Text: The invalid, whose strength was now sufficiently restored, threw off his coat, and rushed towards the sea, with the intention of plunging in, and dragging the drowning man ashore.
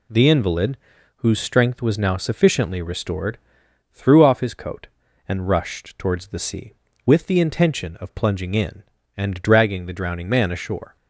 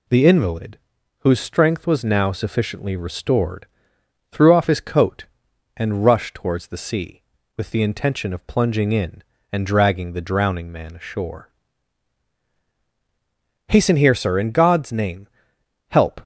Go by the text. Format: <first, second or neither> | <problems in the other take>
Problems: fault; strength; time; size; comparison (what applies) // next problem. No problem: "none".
first | goes on to say "Hasten here Sir in God's name help"; strong; from 13.6 s on; 2.5 s long